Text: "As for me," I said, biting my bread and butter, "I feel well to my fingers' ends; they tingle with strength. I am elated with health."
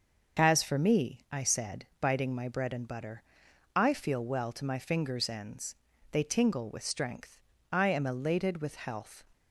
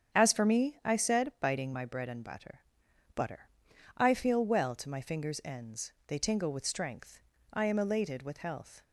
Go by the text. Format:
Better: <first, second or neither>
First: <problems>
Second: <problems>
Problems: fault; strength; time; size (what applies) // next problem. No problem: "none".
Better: first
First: starts louder than the rest; until 1.4 s; 6 dB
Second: starts louder than the rest; strong; until 1.2 s; 8 dB // says "butter" twice; at 3.1 s